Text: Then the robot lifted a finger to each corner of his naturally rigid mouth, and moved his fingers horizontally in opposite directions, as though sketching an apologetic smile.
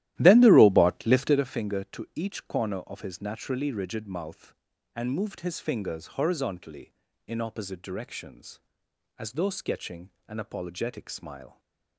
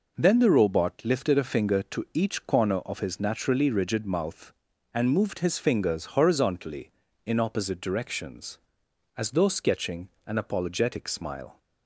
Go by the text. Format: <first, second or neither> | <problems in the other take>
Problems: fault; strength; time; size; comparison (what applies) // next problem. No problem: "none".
second | starts louder than the rest; strong; until 1.5 s; 14.5 dB // pauses between "sketching" and "an"; slight; at 10.1 s; 0.16 s long; slight in the second // stays silent after the last word; slight; from 11.4 s on; 0.5 s long